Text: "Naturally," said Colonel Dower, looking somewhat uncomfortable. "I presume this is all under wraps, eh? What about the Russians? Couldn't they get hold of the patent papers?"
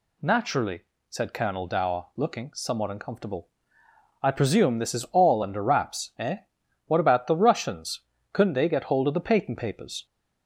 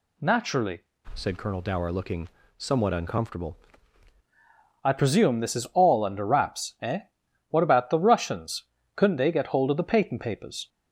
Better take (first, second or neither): first